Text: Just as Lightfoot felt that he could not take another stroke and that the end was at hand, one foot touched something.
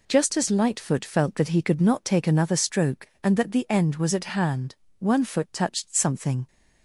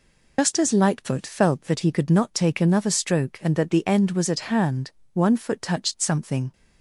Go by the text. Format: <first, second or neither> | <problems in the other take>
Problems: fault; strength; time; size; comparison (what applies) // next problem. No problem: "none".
first | loses the start of "Just"; at 0.3 s; 115 ms